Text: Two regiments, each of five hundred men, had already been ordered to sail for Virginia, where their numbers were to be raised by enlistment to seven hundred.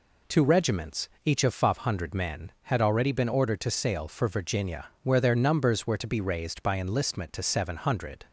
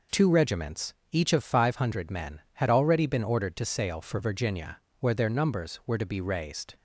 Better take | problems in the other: first | stops before "by enlistment to seven hundred"; at 6.7 s

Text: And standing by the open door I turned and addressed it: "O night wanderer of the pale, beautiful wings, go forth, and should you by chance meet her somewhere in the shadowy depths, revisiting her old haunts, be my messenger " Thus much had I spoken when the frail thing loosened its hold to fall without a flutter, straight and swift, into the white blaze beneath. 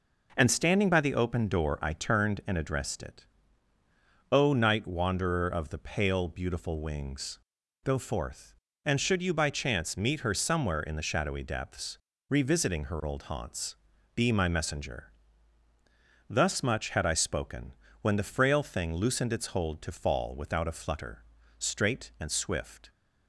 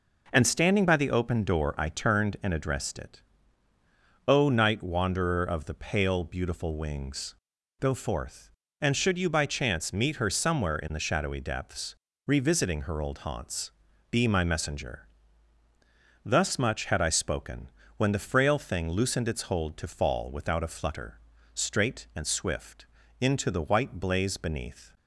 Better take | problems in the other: second | pauses between "spoken" and "when"; slight; at 17.7 s; 0.26 s long; slight in the second // stops before "into the white blaze beneath"; at 22.8 s

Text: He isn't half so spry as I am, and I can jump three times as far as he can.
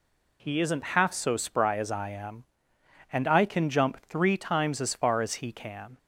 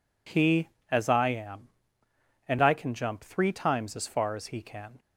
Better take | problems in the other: first | skips "isn't half so spry"; at 0.7 s

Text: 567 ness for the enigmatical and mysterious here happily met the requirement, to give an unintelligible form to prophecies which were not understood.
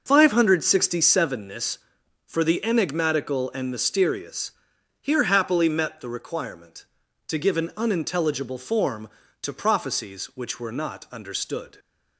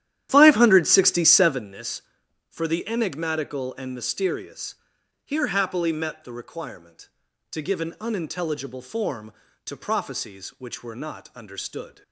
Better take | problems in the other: first | starts louder than the rest; strong; until 1.7 s; 11.5 dB // pauses between "mysterious" and "here"; noticeable; at 4.7 s; 0.48 s long; noticeable in the first

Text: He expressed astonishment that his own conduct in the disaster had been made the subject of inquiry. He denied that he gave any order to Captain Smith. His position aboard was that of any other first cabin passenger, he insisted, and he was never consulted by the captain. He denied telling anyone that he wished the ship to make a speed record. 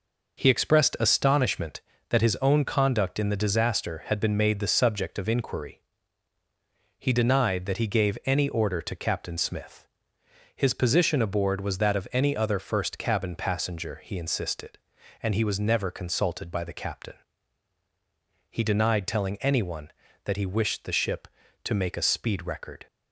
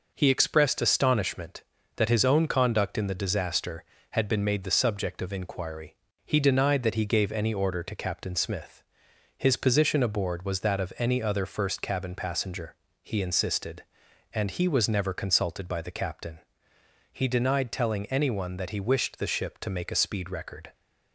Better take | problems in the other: neither | none

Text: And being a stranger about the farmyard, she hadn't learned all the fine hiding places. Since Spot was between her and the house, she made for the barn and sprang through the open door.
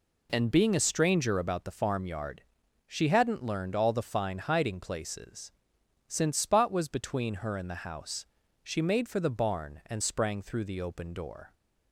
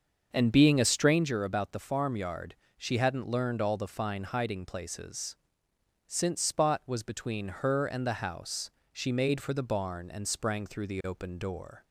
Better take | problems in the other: first | starts louder than the rest; until 1.3 s; 6.5 dB

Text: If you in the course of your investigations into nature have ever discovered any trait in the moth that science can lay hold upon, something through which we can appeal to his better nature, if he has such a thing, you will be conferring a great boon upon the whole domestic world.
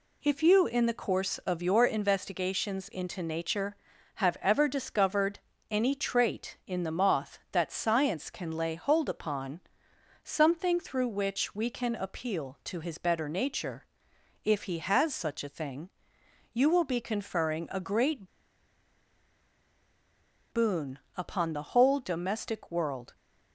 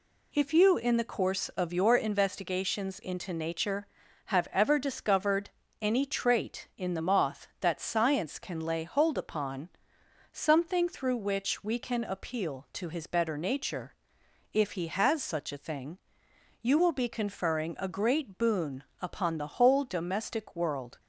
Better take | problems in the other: second | pauses between "discovered" and "any"; slight; at 5.3 s; 0.30 s long; slight in the second // pauses between "great" and "boon"; strong; at 18.2 s; 2.2 s long // pauses between "boon" and "upon"; slight; at 20.9 s; 0.18 s long; slight in the second

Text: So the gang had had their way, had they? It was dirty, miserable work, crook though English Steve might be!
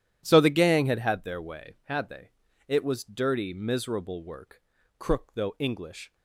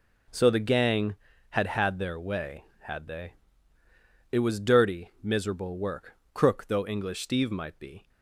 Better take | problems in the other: second | starts louder than the rest; strong; until 1.2 s; 11 dB // stops before "Steve might be"; at 6.1 s

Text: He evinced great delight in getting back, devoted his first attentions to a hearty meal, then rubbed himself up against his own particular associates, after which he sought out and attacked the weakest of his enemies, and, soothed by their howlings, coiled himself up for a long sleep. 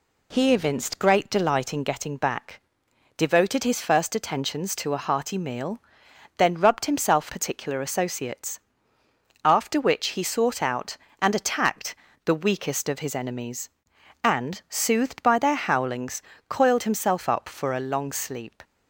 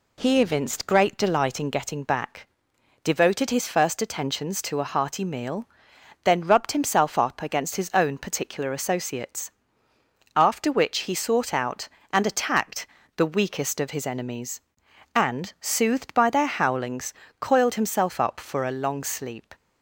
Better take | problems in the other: second | skips "up against his own"; at 7.2 s // pauses between "attacked" and "the"; slight; at 11.9 s; 0.28 s long; slight in the second

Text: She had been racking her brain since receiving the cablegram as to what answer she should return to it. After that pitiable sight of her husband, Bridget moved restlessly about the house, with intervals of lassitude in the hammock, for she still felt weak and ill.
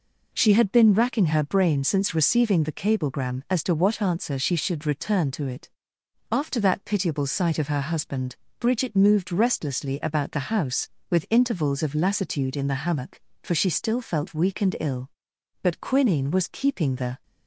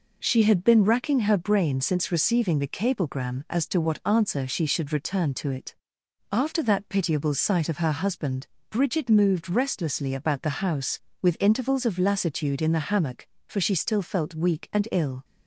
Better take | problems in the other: second | goes on to say "But quinine was keeping the"; from 15.6 s on; 1.6 s long

